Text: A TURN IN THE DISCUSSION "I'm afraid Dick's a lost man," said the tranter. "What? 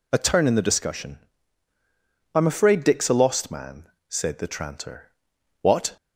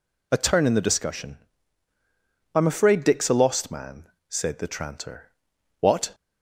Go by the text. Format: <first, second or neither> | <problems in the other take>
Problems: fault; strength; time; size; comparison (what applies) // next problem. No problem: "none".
neither | pauses between "DISCUSSION" and "I'm"; the same in both